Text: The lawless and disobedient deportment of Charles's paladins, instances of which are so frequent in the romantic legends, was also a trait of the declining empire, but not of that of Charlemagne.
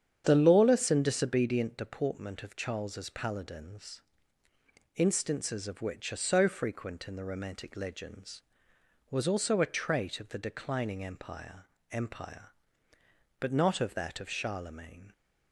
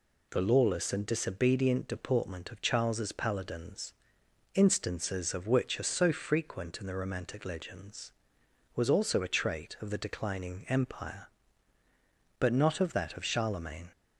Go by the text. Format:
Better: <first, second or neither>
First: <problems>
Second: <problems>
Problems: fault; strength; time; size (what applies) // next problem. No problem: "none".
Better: second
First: starts louder than the rest; strong; until 1.2 s; 8.5 dB // says "empire" twice; at 11.9 s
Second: none